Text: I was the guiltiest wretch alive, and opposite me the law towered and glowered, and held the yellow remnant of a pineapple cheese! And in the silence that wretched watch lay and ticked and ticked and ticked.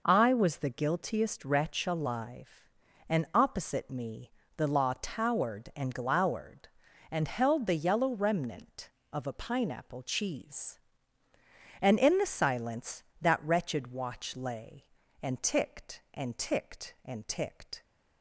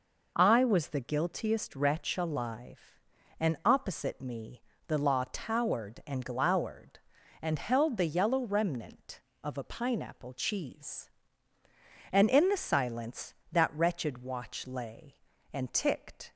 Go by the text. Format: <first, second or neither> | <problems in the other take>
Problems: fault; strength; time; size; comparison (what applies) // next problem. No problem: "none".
first | pauses between "me" and "the"; slight; at 4.6 s; 0.26 s long; slight in the first // stops before "and ticked and ticked"; at 16.3 s